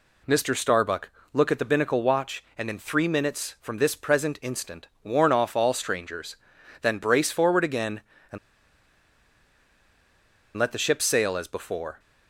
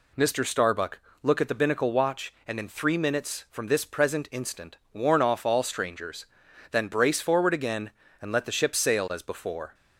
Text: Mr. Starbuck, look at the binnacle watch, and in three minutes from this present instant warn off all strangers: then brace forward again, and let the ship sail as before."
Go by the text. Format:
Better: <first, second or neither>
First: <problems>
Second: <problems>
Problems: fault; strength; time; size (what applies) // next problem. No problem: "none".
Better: second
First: pauses between "instant" and "warn"; slight; at 4.8 s; 0.16 s long // pauses between "and" and "let"; strong; at 8.3 s; 2.1 s long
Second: pauses between "instant" and "warn"; slight; at 4.7 s; 0.16 s long